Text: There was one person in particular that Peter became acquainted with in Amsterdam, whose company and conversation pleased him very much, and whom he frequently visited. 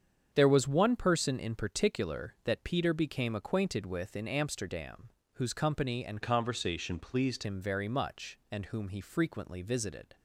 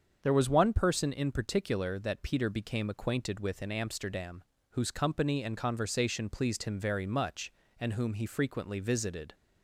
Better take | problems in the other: second | starts louder than the rest; strong; until 1.3 s; 7.5 dB; also in the second // changes voice from "conversation" to "pleased"; from 6.2 to 7.4 s; 1.2 s long

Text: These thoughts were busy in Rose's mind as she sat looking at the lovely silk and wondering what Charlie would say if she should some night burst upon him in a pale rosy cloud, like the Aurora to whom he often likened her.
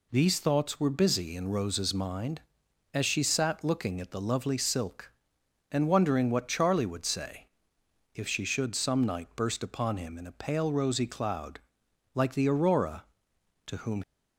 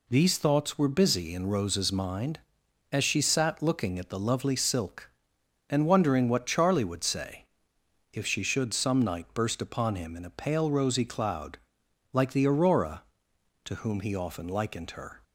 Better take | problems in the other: second | pauses between "say" and "if"; noticeable; at 7.4 s; 0.68 s long; noticeable in the second // stops before "he often likened her"; at 14.0 s

